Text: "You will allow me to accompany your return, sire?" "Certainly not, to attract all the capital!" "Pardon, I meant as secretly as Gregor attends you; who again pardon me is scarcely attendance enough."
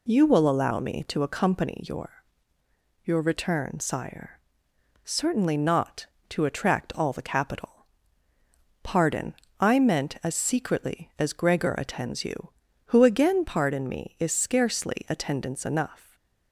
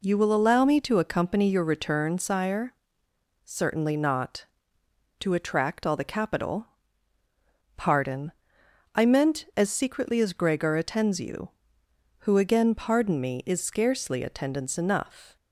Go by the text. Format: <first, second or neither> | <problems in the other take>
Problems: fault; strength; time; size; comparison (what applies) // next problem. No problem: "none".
second | says "your" twice; at 3.0 s // stays silent after the last word; slight; from 16.0 s on; 0.5 s long